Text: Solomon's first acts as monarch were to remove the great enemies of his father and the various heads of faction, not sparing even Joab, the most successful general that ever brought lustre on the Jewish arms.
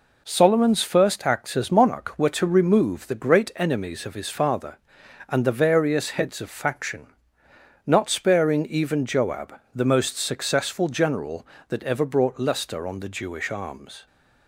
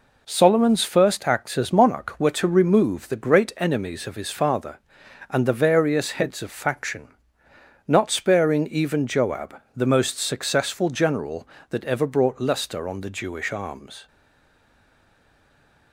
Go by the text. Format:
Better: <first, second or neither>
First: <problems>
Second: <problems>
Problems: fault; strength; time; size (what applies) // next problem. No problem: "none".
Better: first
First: none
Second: stays silent after the last word; noticeable; from 14.0 s on; 1.9 s long